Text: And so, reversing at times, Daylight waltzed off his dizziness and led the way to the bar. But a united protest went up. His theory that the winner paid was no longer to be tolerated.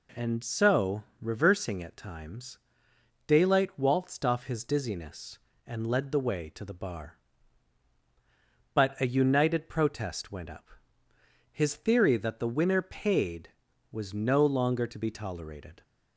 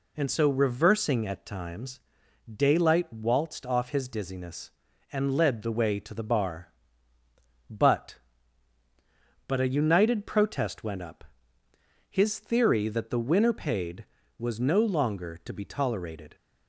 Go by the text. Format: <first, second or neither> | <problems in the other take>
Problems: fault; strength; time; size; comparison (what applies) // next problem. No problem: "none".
first | says "But" twice; at 9.4 s